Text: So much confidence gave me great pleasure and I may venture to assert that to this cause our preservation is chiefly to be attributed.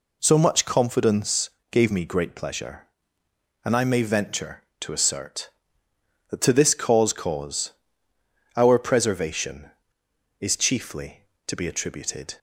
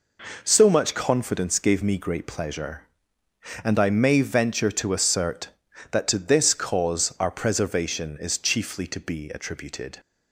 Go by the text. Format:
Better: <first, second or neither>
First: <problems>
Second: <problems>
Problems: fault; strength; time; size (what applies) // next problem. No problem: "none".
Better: second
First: pauses between "confidence" and "gave"; slight; at 1.4 s; 0.24 s long // says "cause" twice; at 7.1 s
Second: none